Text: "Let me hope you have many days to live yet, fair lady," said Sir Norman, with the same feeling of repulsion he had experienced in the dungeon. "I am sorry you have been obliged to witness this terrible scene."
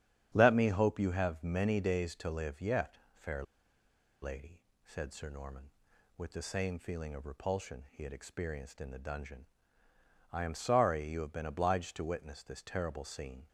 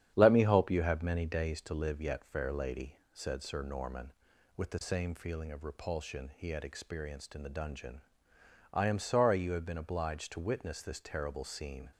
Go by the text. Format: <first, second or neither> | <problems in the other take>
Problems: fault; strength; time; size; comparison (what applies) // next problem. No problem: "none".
second | starts louder than the rest; strong; until 1.3 s; 9 dB; strong in the second // pauses between "fair" and "lady"; noticeable; at 3.4 s; 0.79 s long